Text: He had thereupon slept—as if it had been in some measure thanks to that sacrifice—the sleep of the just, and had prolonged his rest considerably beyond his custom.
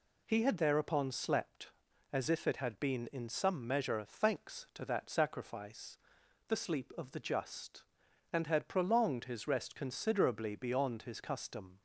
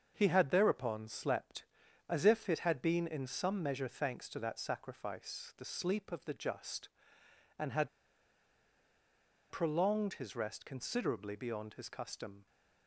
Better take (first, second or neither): first